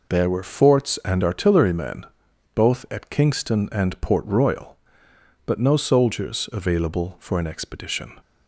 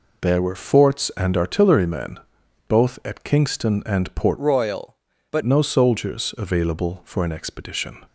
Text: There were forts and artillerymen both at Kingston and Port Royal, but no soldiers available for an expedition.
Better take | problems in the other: first | pauses between "artillerymen" and "both"; noticeable; at 2.1 s; 0.50 s long; noticeable in the first // changes voice from "Royal" to "but"; from 4.3 to 5.4 s; 1.1 s long

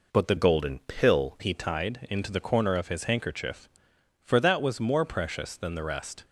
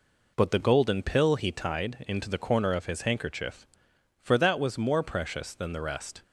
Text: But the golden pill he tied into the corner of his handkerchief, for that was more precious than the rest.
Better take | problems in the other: second | changes voice from "golden" to "pill"; from 0.3 to 1.3 s; 1.0 s long

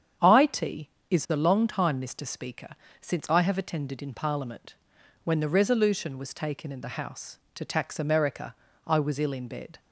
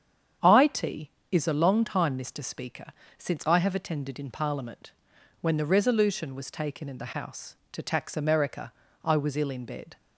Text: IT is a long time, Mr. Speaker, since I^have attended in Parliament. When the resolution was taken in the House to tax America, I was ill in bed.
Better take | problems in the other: neither | starts louder than the rest; strong; the same in both

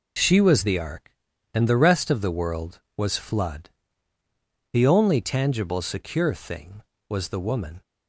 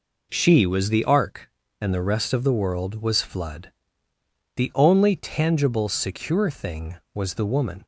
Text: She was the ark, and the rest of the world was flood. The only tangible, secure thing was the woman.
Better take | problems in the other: neither | none

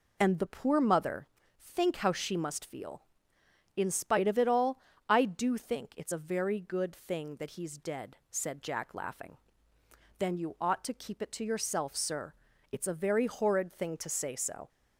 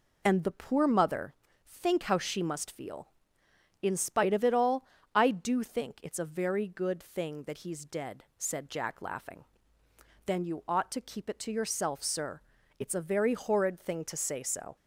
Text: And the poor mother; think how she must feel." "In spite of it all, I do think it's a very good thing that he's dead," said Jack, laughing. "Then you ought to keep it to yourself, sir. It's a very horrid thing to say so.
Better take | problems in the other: neither | none

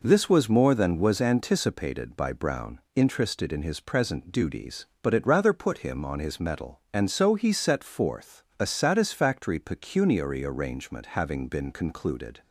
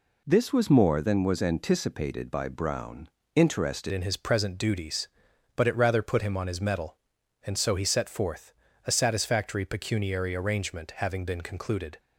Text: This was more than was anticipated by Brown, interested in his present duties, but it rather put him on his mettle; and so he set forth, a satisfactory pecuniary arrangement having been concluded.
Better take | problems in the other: first | changes voice at "in"; from 3.9 s on; 8.0 s long

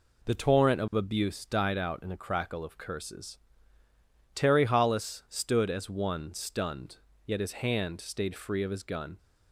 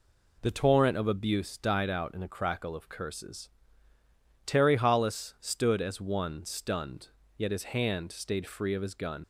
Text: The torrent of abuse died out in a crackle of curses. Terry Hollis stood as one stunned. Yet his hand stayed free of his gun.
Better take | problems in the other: first | leaves "gun" unfinished; at 9.2 s; 45 ms

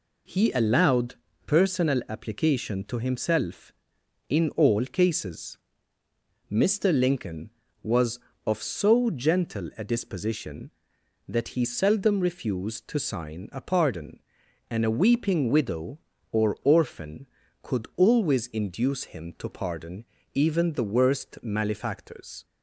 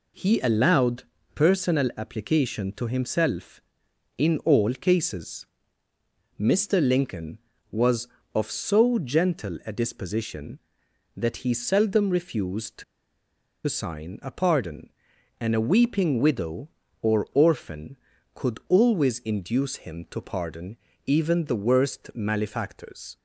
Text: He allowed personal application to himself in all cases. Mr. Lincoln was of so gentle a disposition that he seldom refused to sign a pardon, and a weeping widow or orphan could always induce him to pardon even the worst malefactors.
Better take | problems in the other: first | pauses between "allowed" and "personal"; slight; at 1.0 s; 0.32 s long; slight in the first // pauses between "to" and "sign"; noticeable; at 12.8 s; 0.83 s long // pauses between "pardon" and "even"; slight; at 20.7 s; 0.28 s long; slight in the first

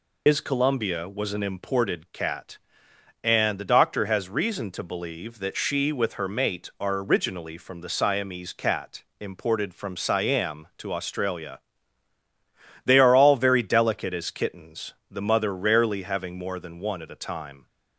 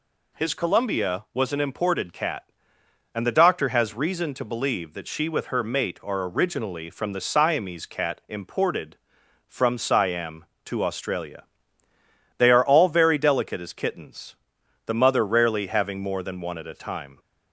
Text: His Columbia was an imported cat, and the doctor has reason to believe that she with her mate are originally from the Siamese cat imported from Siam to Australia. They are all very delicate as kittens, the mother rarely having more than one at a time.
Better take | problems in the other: second | loses the start of "His"; at 0.2 s; 65 ms // pauses between "cat" and "imported"; slight; at 9.0 s; 0.18 s long

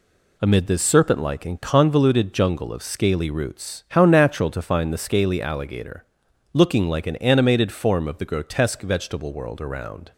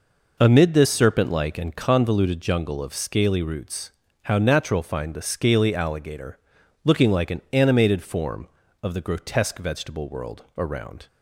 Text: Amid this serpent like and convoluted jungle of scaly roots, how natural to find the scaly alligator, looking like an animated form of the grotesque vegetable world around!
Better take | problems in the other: first | skips "to"; at 4.8 s

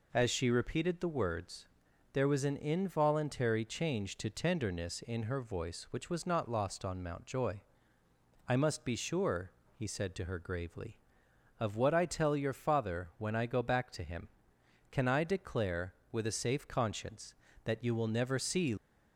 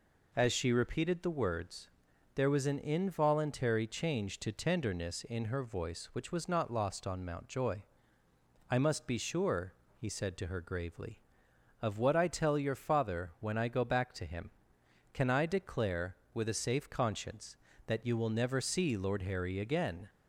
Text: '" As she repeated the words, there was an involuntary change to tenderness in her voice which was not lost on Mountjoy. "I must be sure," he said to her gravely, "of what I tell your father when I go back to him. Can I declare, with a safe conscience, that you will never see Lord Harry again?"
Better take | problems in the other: second | stops before "Lord Harry again"; at 18.7 s

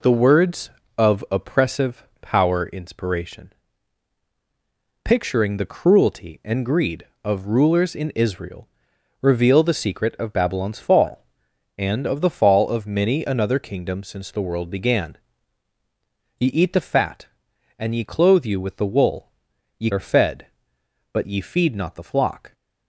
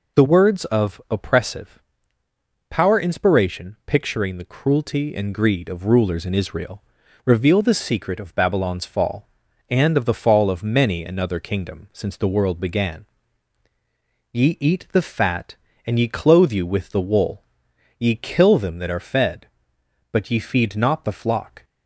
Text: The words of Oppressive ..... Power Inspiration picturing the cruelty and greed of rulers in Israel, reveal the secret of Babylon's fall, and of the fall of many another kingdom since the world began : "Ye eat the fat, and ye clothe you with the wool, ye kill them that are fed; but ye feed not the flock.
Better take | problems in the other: second | pauses between "Inspiration" and "picturing"; strong; at 3.5 s; 1.5 s long // skips "kill them that"; at 19.9 s

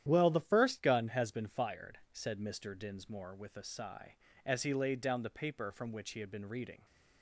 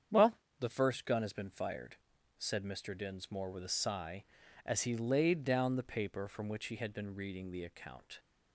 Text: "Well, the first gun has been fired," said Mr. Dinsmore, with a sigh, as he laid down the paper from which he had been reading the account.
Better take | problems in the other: second | starts louder than the rest; strong; until 1.0 s; 10.5 dB; strong in the second // stops before "the account"; at 6.8 s

